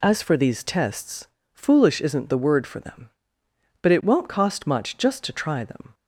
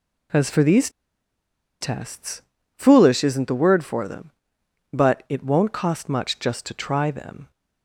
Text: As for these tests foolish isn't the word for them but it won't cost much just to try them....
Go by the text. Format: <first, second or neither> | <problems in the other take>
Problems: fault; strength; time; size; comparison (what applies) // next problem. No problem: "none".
first | pauses between "these" and "tests"; noticeable; at 0.8 s; 0.92 s long // pauses between "tests" and "foolish"; slight; at 2.4 s; 0.34 s long; slight in the first